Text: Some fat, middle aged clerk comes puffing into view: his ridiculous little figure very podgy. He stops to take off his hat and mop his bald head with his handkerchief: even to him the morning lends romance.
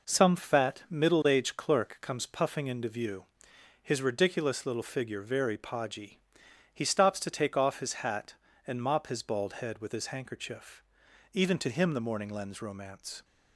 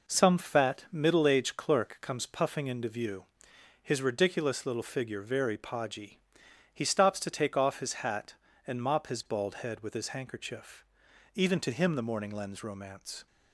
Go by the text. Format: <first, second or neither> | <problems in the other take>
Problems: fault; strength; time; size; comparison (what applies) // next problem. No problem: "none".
neither | none